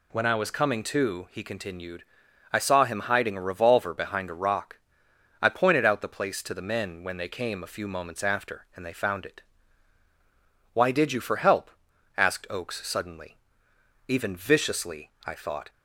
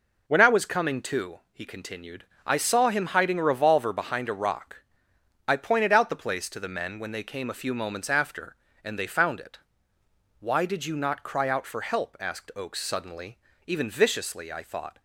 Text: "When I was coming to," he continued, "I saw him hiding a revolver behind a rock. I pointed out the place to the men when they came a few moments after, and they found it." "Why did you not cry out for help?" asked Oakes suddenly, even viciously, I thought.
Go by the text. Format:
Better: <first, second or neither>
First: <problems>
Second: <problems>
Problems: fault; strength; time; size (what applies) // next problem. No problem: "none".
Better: second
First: skips "not cry out"; at 11.2 s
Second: none